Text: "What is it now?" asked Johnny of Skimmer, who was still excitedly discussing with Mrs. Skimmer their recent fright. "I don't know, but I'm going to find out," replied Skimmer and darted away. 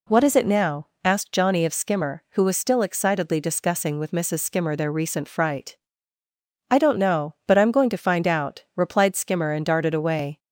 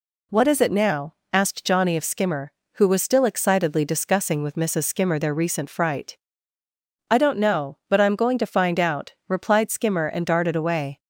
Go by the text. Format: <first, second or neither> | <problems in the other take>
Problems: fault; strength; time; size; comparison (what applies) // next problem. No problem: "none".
neither | none